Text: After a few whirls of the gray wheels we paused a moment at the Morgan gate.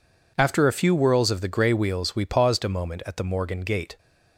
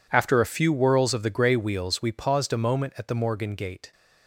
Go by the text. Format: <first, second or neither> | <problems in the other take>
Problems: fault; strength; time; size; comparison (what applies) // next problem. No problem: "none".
first | gets quieter; strong; throughout; 17 dB